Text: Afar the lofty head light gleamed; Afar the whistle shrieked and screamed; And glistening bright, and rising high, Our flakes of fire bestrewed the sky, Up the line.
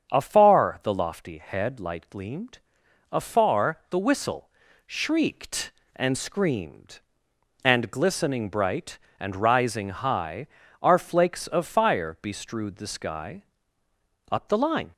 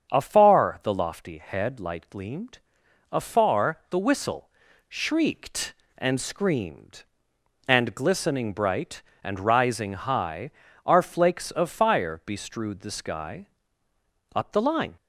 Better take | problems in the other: neither | starts louder than the rest; strong; the same in both // pauses between "whistle" and "shrieked"; the same in both

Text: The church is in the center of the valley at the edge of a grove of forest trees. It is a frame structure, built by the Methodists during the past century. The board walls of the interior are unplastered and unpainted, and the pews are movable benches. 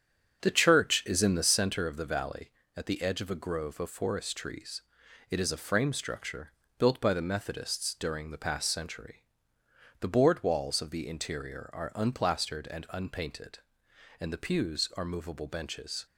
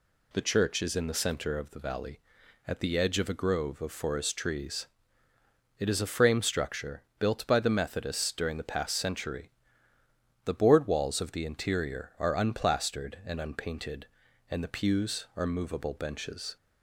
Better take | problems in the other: second | starts louder than the rest; strong; until 1.9 s; 8 dB

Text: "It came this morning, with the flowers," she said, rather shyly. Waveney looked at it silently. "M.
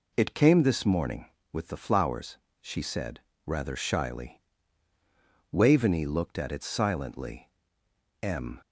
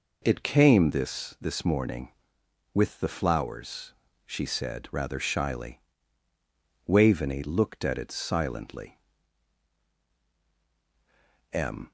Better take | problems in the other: first | says "this" twice; at 1.4 s

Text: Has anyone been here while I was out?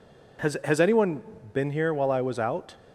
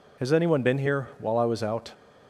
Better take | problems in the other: second | says "Has" twice; at 0.6 s // pauses between "anyone" and "been"; slight; at 1.2 s; 0.30 s long

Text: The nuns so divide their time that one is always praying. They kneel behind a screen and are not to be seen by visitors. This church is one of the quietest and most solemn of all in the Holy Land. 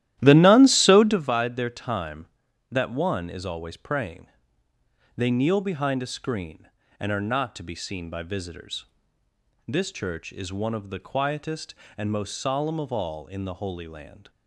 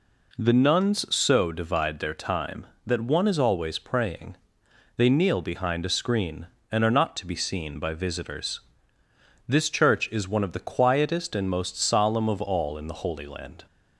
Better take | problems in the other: second | starts louder than the rest; strong; until 1.3 s; 13.5 dB

